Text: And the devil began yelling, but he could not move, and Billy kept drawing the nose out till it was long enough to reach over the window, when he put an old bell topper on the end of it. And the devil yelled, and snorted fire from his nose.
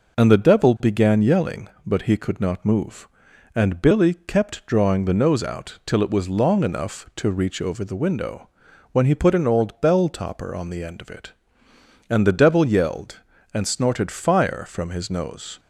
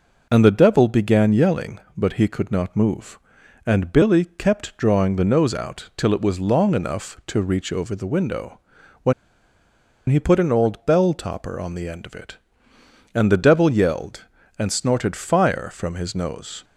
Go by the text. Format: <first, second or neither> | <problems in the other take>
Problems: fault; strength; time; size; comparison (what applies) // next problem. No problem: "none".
first | pauses between "when" and "he"; noticeable; at 9.1 s; 0.96 s long